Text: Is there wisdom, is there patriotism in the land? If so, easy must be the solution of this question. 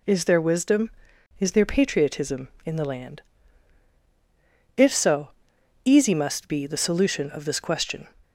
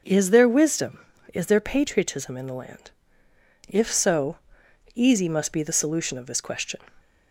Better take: neither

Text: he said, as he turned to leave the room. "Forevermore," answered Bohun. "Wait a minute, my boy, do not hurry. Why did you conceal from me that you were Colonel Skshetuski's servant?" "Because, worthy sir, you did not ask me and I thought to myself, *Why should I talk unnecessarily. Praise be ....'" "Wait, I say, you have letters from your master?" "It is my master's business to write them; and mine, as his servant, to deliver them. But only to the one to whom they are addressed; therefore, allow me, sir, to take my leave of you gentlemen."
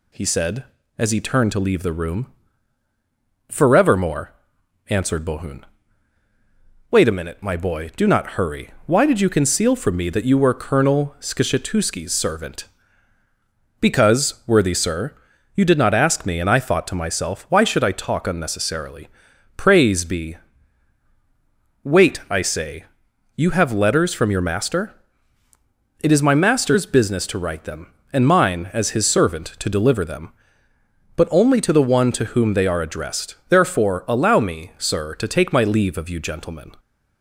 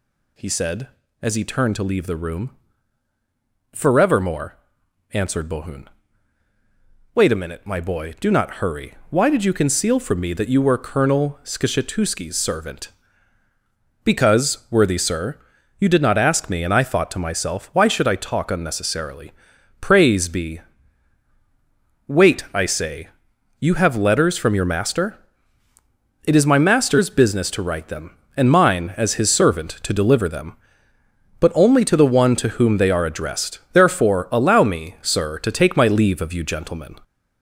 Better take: first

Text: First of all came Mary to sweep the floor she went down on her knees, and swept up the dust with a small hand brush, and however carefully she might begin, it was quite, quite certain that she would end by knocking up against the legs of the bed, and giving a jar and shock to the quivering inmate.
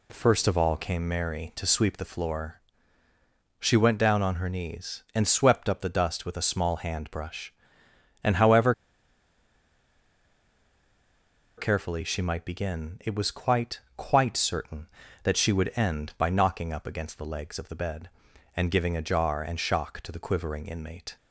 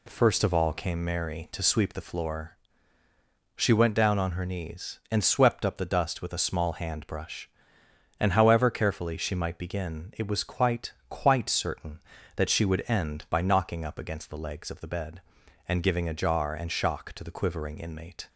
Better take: second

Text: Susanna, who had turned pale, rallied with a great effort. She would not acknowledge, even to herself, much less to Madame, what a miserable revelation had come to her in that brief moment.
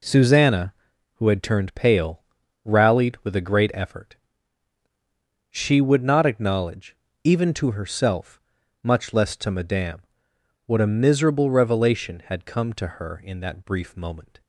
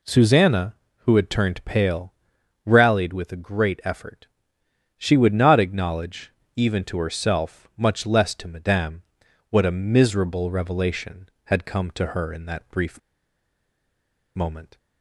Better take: first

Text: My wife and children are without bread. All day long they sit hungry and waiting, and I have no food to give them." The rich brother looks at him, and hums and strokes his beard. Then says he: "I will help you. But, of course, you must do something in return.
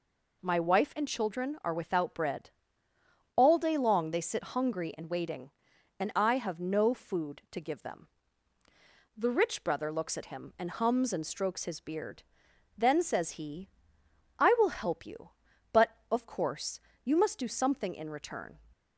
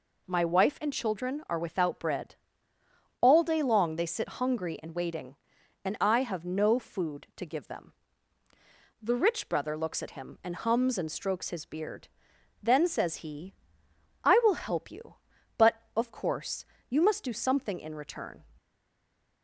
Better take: first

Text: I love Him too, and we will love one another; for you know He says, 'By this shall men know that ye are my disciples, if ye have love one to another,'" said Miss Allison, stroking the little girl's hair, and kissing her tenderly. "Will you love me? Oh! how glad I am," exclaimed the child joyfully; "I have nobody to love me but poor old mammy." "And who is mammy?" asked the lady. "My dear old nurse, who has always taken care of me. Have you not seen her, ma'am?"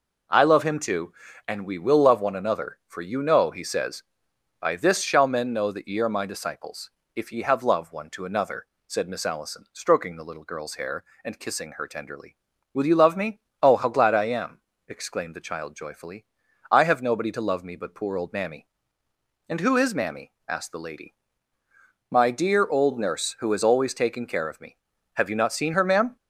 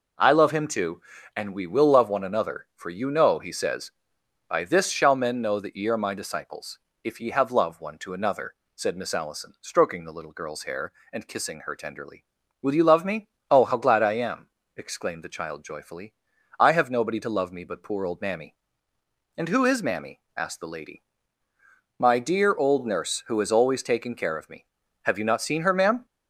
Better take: neither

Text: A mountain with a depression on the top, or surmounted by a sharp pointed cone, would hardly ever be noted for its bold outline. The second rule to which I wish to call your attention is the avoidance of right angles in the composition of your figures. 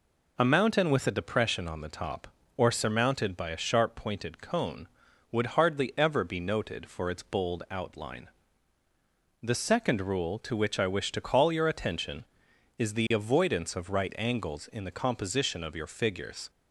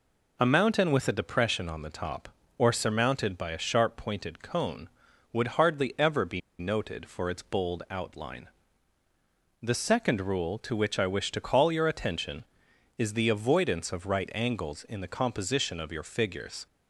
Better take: first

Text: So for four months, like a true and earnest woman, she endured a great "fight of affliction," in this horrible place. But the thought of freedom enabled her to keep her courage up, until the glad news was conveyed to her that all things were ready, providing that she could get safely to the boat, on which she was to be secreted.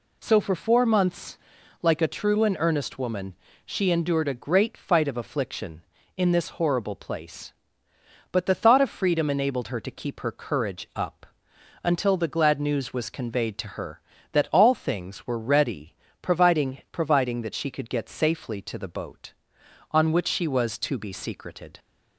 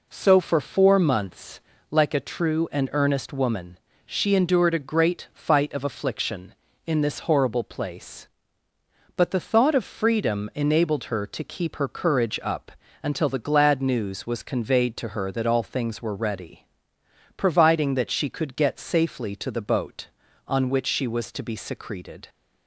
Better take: second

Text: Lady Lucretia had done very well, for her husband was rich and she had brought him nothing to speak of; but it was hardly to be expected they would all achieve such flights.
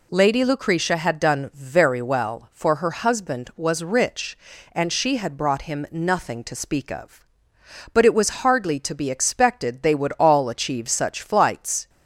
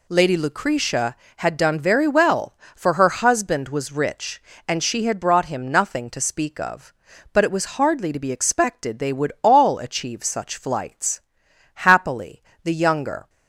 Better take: first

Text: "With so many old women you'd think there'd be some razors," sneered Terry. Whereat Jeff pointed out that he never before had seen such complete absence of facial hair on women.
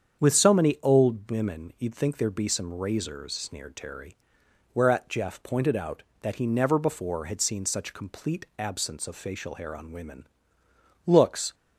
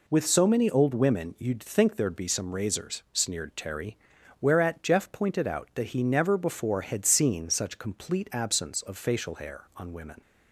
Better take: second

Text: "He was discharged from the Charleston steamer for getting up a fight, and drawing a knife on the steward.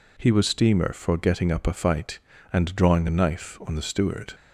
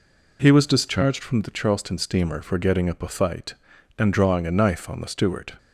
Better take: second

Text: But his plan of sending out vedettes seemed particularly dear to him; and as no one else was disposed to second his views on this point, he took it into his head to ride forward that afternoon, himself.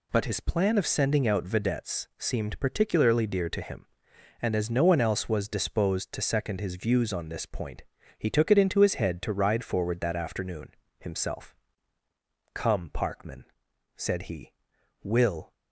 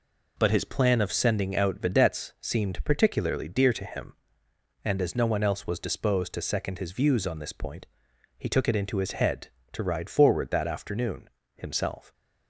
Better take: second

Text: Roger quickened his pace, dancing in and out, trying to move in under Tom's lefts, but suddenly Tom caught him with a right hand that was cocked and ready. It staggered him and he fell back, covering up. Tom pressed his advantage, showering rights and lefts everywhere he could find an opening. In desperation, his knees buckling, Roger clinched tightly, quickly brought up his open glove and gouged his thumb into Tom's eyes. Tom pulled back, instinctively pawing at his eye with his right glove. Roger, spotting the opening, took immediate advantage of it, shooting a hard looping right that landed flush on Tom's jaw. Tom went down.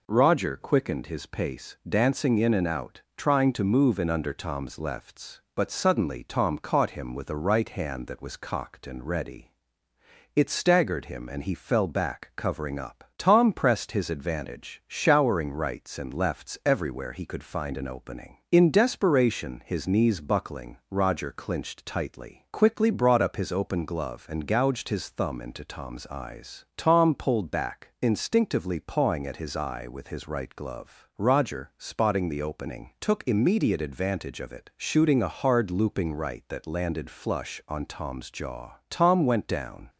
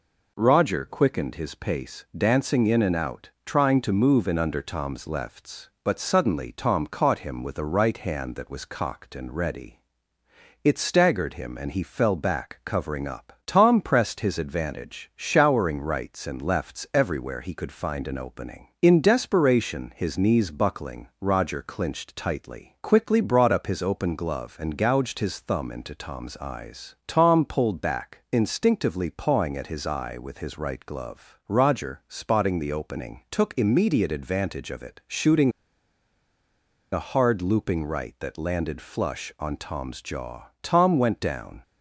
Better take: first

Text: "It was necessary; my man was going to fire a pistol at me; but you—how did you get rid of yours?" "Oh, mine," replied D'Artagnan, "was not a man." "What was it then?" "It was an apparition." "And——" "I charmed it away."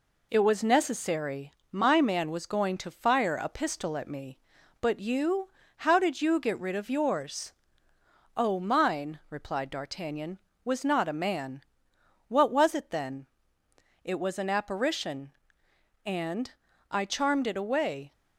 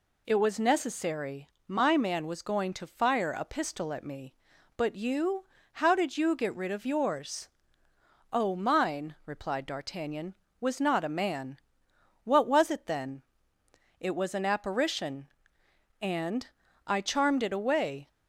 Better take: second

